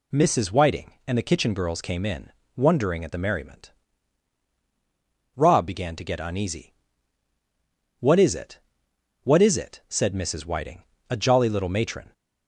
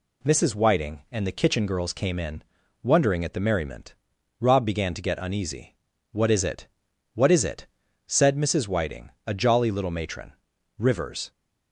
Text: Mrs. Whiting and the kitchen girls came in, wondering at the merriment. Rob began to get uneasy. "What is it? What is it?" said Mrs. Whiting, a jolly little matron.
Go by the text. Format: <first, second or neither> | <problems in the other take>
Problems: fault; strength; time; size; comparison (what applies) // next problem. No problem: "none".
first | goes on to say "Rivers"; from 10.7 s on; 0.54 s long